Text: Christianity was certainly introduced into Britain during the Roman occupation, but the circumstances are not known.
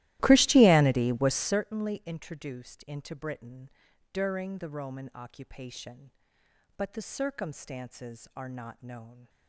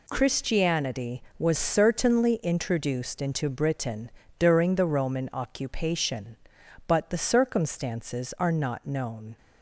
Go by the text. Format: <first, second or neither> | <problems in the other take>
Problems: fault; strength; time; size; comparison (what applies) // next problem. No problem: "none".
second | starts louder than the rest; strong; until 1.7 s; 16 dB // pauses between "Britain" and "during"; at 3.7 s; 0.42 s long; slight in the second